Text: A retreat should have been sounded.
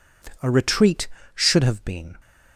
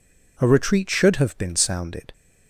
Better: second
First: stops before "sounded"; at 2.1 s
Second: none

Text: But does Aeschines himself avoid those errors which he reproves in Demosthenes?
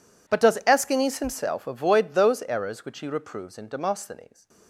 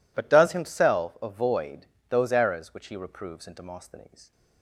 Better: first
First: none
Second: skips "Aeschines"; at 0.5 s // pauses between "avoid" and "those"; slight; at 1.8 s; 0.20 s long

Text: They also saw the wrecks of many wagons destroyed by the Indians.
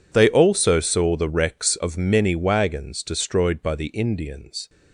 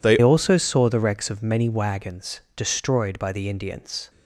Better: first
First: none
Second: changes voice at "also"; from 0.2 s on; 3.8 s long

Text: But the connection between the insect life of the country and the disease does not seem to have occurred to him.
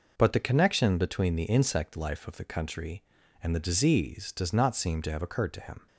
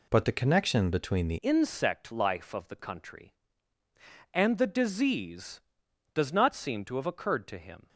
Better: first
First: none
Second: changes voice at "insect"; from 1.4 s on; 6.4 s long

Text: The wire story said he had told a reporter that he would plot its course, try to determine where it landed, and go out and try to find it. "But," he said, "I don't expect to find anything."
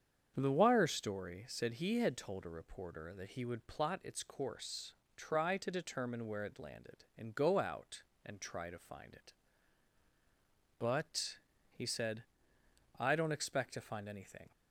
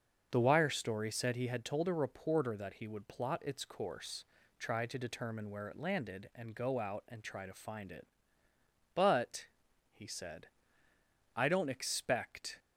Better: first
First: starts louder than the rest; strong; until 1.3 s; 7.5 dB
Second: starts louder than the rest; until 1.3 s; 6.5 dB // stops before "to find anything"; at 12.5 s

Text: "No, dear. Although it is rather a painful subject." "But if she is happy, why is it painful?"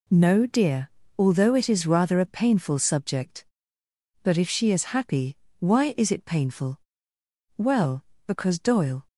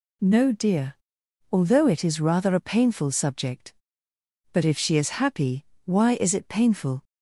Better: second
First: goes on to say "Well because Doyle"; from 7.5 s on; 1.5 s long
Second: none

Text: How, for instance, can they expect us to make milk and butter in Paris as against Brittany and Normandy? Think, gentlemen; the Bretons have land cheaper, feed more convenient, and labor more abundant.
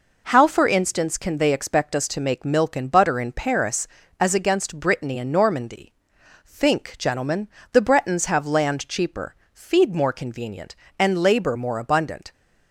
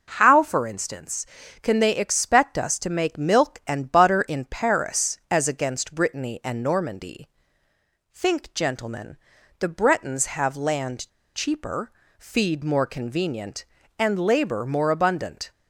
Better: first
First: none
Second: pauses between "land" and "cheaper"; slight; at 11.0 s; 0.25 s long

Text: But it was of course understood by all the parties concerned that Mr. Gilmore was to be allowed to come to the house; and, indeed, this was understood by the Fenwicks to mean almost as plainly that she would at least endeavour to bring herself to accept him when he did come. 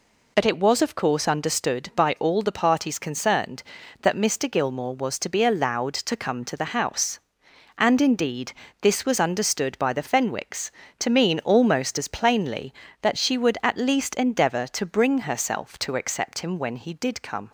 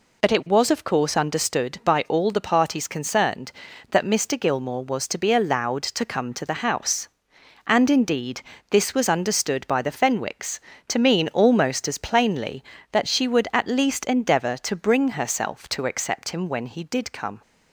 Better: neither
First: none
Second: none

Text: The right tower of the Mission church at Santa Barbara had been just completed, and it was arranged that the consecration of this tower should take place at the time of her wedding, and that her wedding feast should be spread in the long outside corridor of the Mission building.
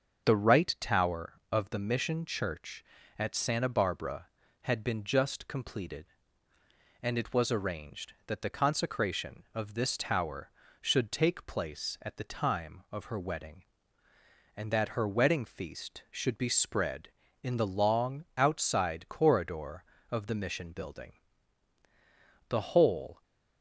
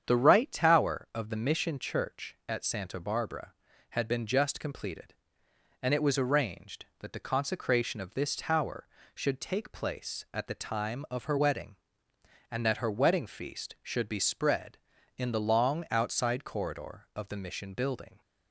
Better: second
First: starts louder than the rest; until 1.3 s; 6.5 dB // goes on to say "The whole"; noticeable; from 22.4 s on; 0.74 s long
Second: starts louder than the rest; strong; until 1.0 s; 8 dB

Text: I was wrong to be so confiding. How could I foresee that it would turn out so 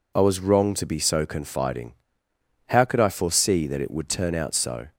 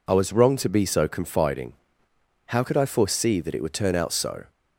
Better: neither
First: none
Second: none

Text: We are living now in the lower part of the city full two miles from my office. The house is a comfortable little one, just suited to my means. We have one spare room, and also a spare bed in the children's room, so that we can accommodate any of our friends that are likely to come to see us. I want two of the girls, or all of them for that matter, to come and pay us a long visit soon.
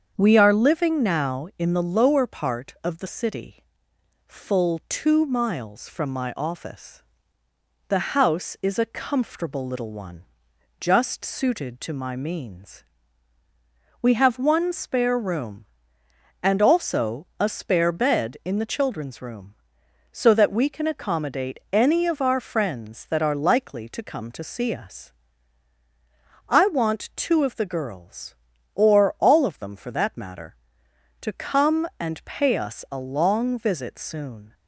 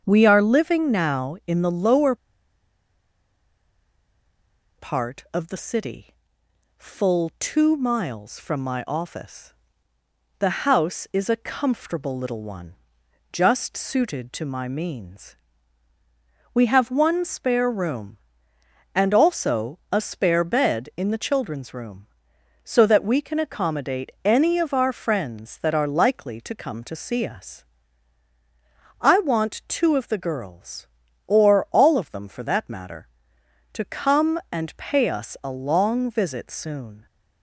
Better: first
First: starts louder than the rest; strong; until 1.1 s; 7 dB // pauses between "city" and "full"; noticeable; at 3.6 s; 0.64 s long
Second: starts louder than the rest; strong; until 1.0 s; 7 dB // pauses between "lower" and "part"; strong; at 2.1 s; 2.6 s long // pauses between "city" and "full"; noticeable; at 6.1 s; 0.64 s long

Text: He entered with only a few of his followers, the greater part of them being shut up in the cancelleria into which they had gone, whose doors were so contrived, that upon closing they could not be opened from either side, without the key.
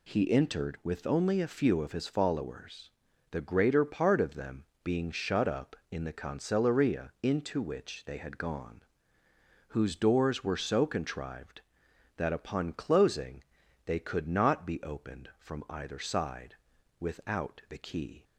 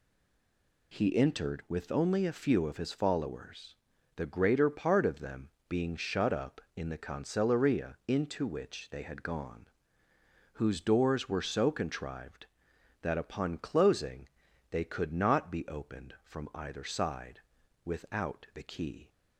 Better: first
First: pauses between "them" and "being"; slight; at 4.6 s; 0.18 s long // pauses between "closing" and "they"; at 13.4 s; 0.40 s long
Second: stays silent before the first word; slight; until 0.9 s; 0.9 s long // pauses between "them" and "being"; slight; at 5.4 s; 0.18 s long // pauses between "closing" and "they"; at 14.2 s; 0.40 s long

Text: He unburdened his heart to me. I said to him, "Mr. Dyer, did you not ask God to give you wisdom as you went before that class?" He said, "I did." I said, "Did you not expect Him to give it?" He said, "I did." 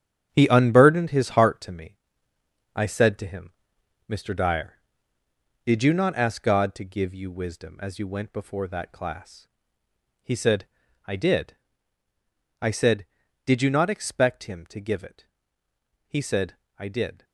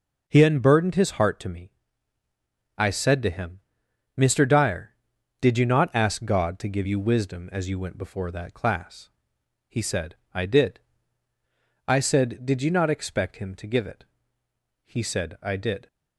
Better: second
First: gets quieter; strong; throughout; 9 dB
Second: none

